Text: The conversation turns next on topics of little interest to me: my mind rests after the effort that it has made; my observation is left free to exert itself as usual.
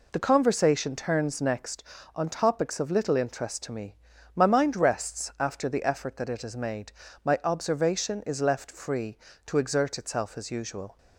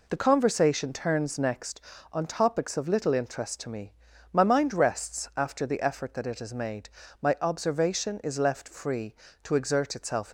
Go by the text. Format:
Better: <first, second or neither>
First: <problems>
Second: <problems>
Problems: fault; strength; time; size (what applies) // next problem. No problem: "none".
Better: first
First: none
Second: stops before "as usual"; at 10.2 s